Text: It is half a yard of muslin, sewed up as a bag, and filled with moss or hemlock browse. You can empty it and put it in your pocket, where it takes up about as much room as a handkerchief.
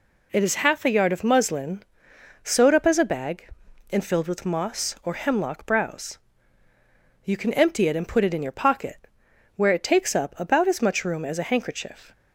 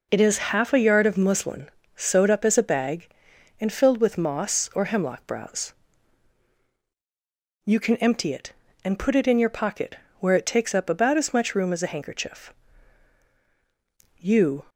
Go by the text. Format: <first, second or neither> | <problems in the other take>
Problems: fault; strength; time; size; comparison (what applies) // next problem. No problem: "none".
first | goes on to say "You"; slight; from 14.1 s on; 0.46 s long